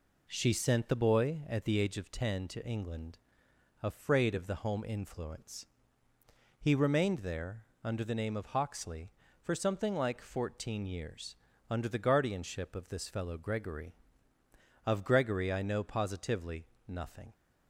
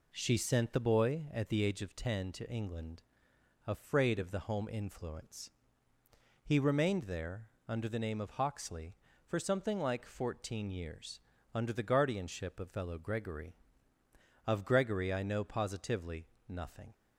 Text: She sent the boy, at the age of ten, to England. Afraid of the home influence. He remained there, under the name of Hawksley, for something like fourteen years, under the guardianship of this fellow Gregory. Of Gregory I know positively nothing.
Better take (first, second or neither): first